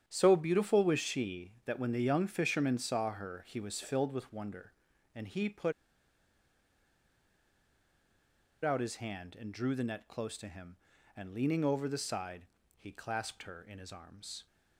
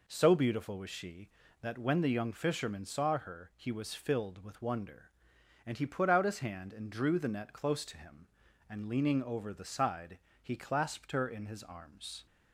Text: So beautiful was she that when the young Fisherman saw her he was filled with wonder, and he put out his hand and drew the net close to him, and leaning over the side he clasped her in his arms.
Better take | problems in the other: second | starts louder than the rest; strong; until 1.0 s; 9 dB // pauses between "put" and "out"; strong; at 5.7 s; 2.9 s long // pauses between "side" and "he"; slight; at 12.4 s; 0.32 s long; slight in the second

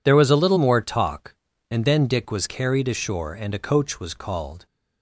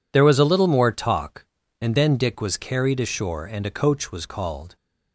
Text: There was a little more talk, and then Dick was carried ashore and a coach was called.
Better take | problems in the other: neither | none

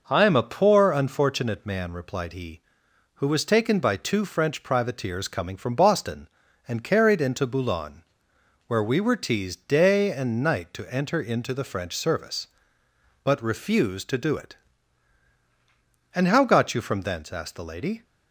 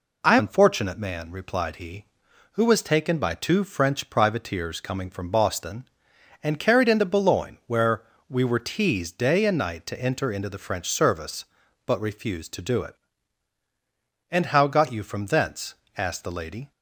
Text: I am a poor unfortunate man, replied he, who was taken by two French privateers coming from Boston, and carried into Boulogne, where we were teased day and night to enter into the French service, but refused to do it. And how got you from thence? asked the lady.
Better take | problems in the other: first | skips "am a poor"; at 0.3 s // pauses between "where" and "we"; slight; at 8.0 s; 0.26 s long

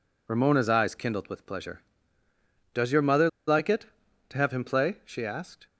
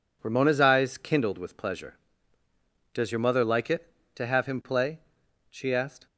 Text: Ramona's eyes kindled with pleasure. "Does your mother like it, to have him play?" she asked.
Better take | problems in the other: second | pauses between "mother" and "like"; slight; at 3.2 s; 0.19 s long

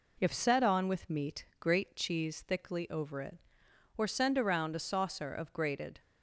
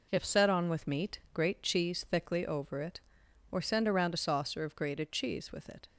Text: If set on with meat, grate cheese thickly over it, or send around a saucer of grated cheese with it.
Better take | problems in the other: second | stops before "cheese with it"; at 6.0 s

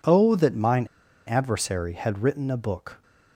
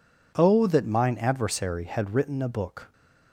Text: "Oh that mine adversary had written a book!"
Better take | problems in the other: second | pauses between "mine" and "adversary"; at 0.8 s; 0.41 s long

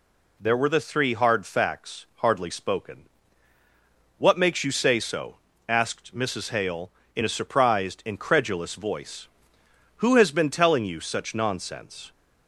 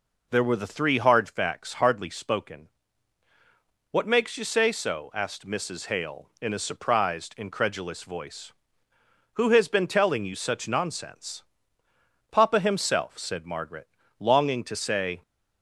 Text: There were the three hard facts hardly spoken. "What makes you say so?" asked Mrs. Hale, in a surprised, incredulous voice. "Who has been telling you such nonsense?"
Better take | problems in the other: first | goes on to say "Papa himself said Margaret longing to say"; strong; from 12.3 s on; 2.8 s long

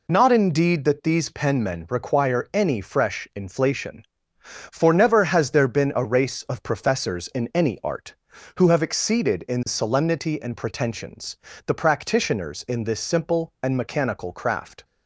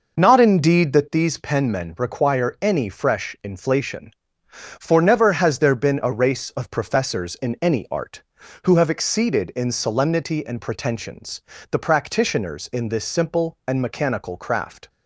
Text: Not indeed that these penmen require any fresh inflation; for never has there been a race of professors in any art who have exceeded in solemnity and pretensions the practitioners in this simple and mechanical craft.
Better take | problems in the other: first | starts louder than the rest; noticeable; until 1.2 s; 5.5 dB // pauses between "pretensions" and "the"; slight; at 11.4 s; 0.30 s long; slight in the first

